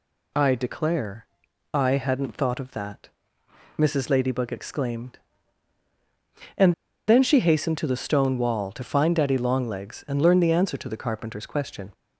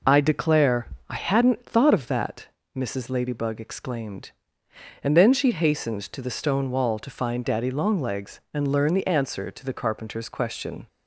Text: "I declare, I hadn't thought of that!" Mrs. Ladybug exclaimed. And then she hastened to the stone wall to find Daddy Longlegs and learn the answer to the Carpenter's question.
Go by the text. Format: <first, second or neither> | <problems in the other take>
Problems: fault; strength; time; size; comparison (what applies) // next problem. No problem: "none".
second | pauses between "And" and "then"; slight; at 6.7 s; 0.35 s long